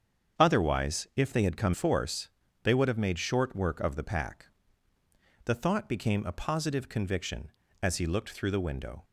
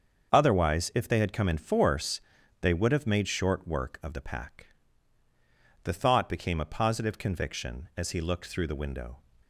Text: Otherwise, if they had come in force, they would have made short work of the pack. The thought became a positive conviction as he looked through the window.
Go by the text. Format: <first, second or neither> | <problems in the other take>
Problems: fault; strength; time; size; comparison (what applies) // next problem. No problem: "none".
second | starts louder than the rest; strong; until 1.4 s; 7.5 dB; also in the second // skips "in"; at 1.7 s